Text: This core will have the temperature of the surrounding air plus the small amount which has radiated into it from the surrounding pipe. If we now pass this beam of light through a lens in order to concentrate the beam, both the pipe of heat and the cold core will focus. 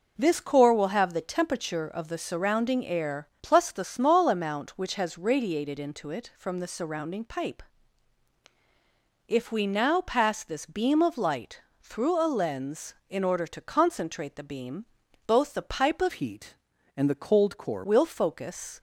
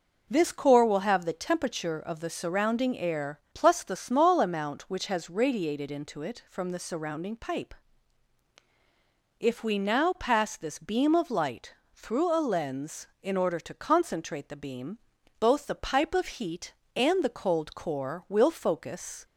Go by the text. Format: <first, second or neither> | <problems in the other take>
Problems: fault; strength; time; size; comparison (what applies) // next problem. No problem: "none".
second | pauses between "light" and "through"; slight; at 11.5 s; 0.22 s long; slight in the second // changes voice from "heat" to "core"; from 16.1 to 17.8 s; 1.7 s long